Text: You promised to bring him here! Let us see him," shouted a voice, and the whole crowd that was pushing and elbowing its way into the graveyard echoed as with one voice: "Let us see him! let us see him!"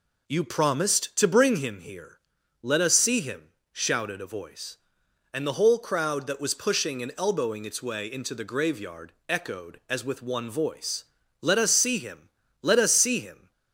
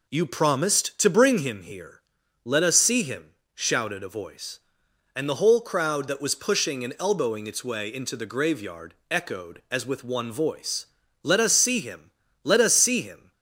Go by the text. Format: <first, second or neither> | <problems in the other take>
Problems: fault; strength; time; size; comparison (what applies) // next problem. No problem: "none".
neither | pauses between "graveyard" and "echoed"; slight; the same in both